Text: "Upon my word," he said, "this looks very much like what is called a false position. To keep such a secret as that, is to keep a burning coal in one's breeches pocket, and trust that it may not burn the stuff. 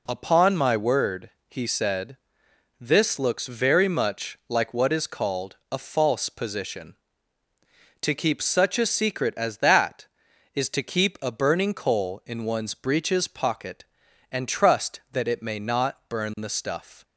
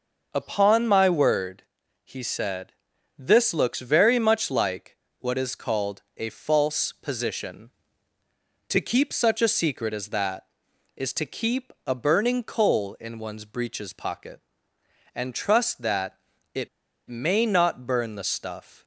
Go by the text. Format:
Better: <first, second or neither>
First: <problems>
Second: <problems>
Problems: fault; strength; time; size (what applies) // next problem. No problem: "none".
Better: first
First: none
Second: starts louder than the rest; until 1.3 s; 6 dB // pauses between "like" and "what"; slight; at 4.9 s; 0.22 s long // pauses between "called" and "a"; slight; at 6.0 s; 0.16 s long // pauses between "that" and "it"; slight; at 16.1 s; 0.34 s long // pauses between "it" and "may"; at 16.6 s; 0.40 s long